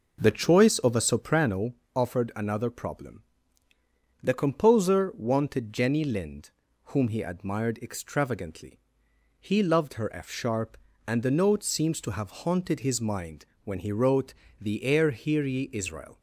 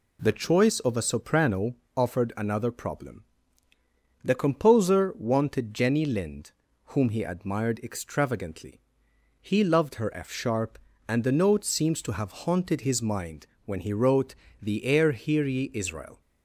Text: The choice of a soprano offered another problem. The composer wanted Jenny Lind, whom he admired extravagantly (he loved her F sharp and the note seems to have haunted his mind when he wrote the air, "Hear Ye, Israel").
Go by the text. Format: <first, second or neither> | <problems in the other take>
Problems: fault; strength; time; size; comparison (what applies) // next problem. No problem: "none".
second | starts louder than the rest; noticeable; until 1.4 s; 5.5 dB // pauses between "soprano" and "offered"; slight; at 1.7 s; 0.20 s long; slight in the second // pauses between "mind" and "when"; slight; at 13.4 s; 0.18 s long; slight in the second // pauses between "wrote" and "the"; slight; at 14.3 s; 0.26 s long; slight in the second